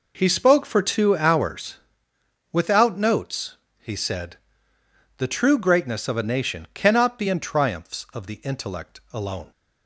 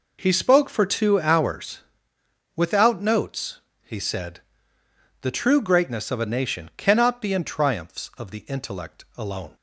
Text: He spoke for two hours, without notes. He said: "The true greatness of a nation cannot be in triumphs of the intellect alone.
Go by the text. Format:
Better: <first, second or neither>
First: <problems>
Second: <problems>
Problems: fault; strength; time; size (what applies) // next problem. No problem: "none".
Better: neither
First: none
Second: none